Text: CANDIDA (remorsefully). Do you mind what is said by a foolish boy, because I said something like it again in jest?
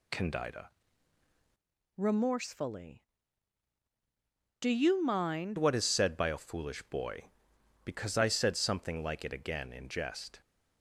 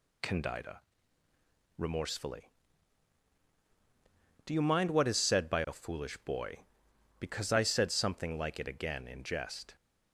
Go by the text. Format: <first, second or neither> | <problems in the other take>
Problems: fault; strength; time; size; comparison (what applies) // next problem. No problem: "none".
second | changes voice from "remorsefully" to "mind"; from 1.9 to 5.5 s; 3.6 s long